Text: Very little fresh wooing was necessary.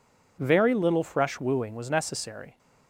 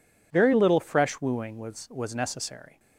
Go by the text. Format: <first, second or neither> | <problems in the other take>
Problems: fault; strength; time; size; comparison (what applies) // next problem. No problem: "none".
first | says "was" twice; at 1.8 s